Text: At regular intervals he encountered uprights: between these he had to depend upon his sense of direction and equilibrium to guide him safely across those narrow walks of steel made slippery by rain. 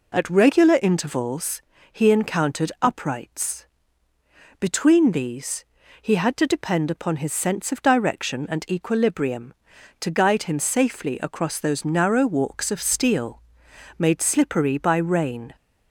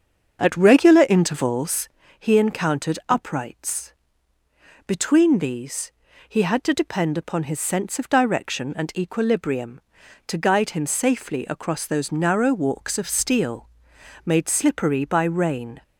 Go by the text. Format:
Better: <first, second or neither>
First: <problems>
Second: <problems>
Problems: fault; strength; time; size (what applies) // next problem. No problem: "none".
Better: first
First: pauses between "intervals" and "he"; slight; at 1.6 s; 0.28 s long // pauses between "these" and "he"; at 5.6 s; 0.38 s long // pauses between "steel" and "made"; noticeable; at 13.4 s; 0.56 s long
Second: starts louder than the rest; until 2.2 s; 7 dB // pauses between "intervals" and "he"; slight; at 1.9 s; 0.28 s long // pauses between "these" and "he"; at 5.9 s; 0.38 s long // pauses between "steel" and "made"; noticeable; at 13.6 s; 0.56 s long